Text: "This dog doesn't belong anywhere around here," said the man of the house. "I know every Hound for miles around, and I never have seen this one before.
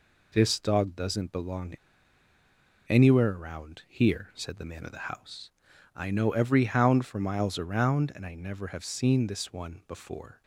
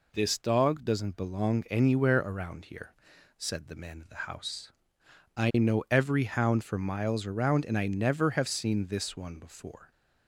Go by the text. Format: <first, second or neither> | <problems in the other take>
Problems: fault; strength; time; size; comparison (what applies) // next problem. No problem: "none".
second | pauses between "belong" and "anywhere"; at 1.7 s; 1.1 s long